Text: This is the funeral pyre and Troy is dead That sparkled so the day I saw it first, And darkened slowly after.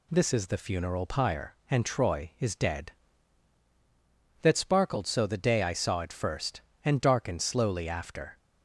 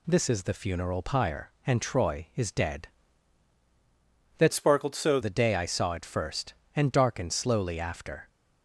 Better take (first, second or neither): first